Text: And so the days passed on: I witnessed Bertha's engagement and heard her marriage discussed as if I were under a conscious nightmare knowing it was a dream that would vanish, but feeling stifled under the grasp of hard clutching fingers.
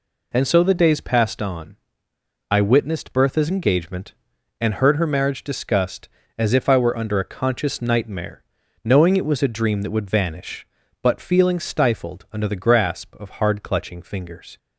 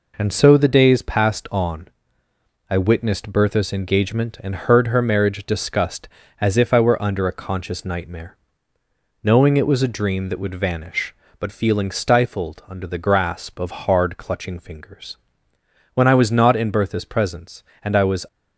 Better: first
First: pauses between "nightmare" and "knowing"; at 8.4 s; 0.40 s long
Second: pauses between "nightmare" and "knowing"; noticeable; at 8.3 s; 0.88 s long // goes on to say "When I was not in Bertha's presence and I was"; strong; from 15.9 s on; 2.3 s long

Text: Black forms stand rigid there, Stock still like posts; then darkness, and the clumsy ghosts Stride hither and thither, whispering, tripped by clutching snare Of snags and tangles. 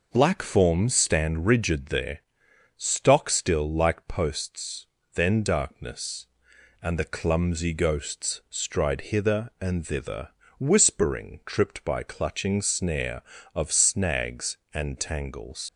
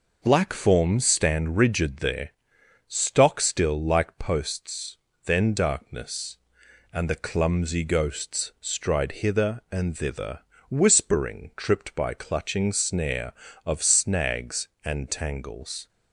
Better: second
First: leaves "tangles" unfinished; at 15.6 s; 85 ms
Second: none

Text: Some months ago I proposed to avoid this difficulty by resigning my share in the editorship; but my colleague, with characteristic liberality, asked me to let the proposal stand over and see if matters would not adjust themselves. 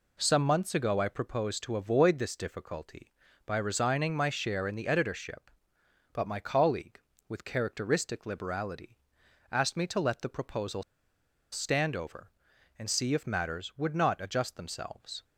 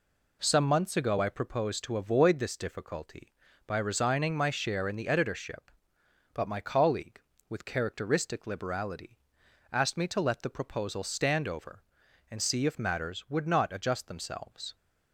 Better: second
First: pauses between "proposal" and "stand"; noticeable; at 10.8 s; 0.70 s long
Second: none

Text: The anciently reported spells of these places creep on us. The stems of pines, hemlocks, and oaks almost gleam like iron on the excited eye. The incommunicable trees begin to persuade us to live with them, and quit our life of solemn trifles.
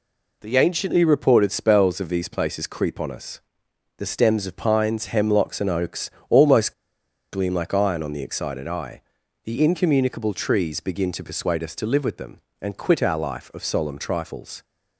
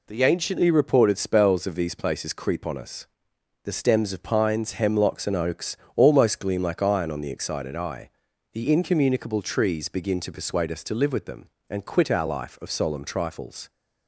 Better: second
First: pauses between "oaks" and "almost"; slight; at 6.1 s; 0.18 s long // pauses between "almost" and "gleam"; noticeable; at 6.7 s; 0.58 s long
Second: pauses between "oaks" and "almost"; slight; at 5.7 s; 0.18 s long

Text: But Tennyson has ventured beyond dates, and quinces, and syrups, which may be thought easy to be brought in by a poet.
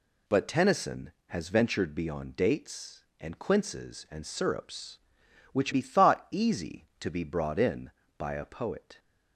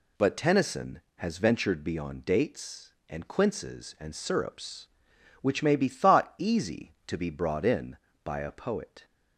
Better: second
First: skips "may"; at 5.7 s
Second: none

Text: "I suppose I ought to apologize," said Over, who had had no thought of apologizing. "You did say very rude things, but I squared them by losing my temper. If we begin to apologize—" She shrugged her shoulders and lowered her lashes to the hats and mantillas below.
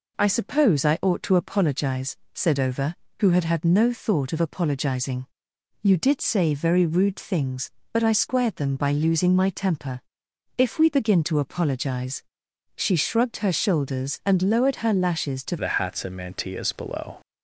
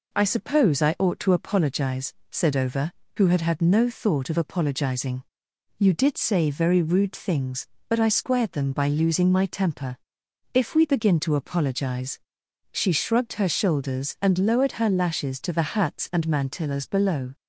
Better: second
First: changes voice at "the"; from 15.5 s on; 1.7 s long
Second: none

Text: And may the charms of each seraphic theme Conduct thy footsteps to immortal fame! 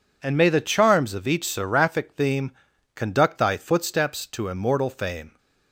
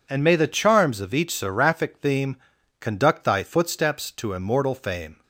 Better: neither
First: pauses between "theme" and "Conduct"; noticeable; at 2.5 s; 0.46 s long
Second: pauses between "theme" and "Conduct"; noticeable; at 2.3 s; 0.46 s long

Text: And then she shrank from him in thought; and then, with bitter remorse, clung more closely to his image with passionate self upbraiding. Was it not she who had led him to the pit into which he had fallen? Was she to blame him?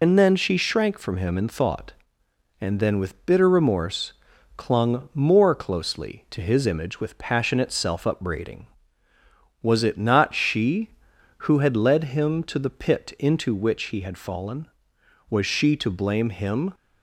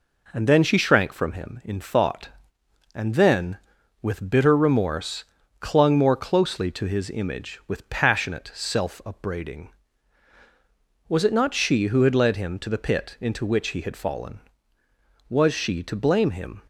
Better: second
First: loses the start of "And"; at 0.0 s; 25 ms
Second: none

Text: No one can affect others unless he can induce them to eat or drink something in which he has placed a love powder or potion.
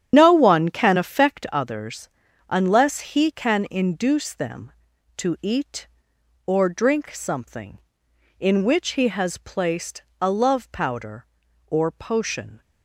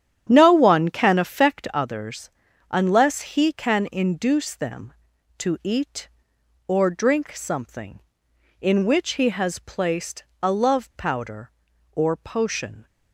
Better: second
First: loses the start of "No"; at 0.1 s; 65 ms // starts louder than the rest; strong; until 1.1 s; 9.5 dB // pauses between "others" and "unless"; at 2.0 s; 0.40 s long // pauses between "placed" and "a"; slight; at 10.0 s; 0.18 s long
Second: starts louder than the rest; strong; until 1.2 s; 9.5 dB // pauses between "others" and "unless"; at 2.2 s; 0.40 s long // pauses between "placed" and "a"; slight; at 10.2 s; 0.18 s long

